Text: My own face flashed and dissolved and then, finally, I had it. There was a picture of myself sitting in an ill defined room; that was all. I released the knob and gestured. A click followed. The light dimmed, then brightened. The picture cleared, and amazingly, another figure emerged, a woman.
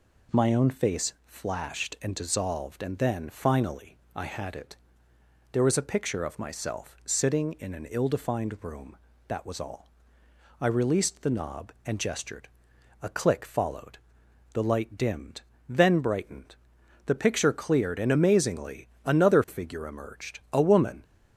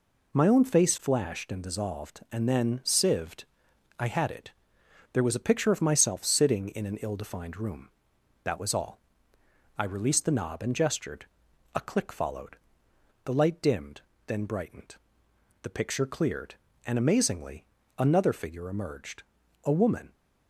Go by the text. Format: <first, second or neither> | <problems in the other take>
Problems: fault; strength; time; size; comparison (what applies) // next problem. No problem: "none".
first | says "sieved" for "finally"; at 2.8 s